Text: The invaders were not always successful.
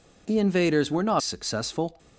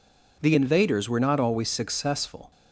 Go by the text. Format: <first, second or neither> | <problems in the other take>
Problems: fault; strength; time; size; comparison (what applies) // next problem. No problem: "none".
second | skips "always"; at 1.2 s